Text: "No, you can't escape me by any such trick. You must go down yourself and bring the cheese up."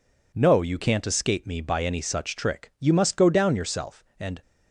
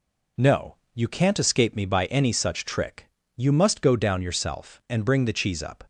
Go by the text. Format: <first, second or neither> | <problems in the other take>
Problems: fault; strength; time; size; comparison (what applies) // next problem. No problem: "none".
second | stops before "bring the cheese up"; at 4.4 s